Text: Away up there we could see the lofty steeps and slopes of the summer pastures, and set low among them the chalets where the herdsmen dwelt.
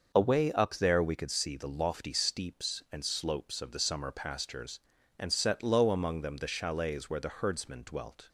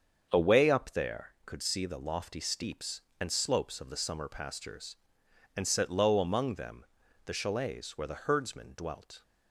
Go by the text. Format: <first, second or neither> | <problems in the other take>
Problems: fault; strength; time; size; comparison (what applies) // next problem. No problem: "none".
first | starts louder than the rest; until 1.3 s; 7 dB; noticeable in the first // skips "we"; at 1.3 s // pauses between "them" and "the"; at 6.8 s; 0.40 s long